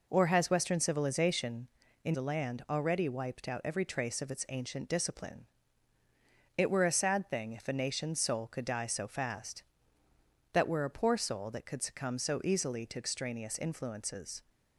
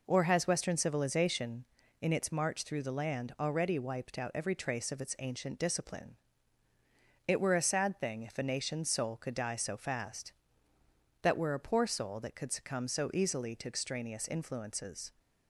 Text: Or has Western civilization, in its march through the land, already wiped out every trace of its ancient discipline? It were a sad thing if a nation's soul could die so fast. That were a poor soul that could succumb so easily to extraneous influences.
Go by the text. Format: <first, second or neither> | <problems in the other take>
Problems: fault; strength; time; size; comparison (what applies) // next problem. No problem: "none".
second | skips "its march through"; at 2.1 s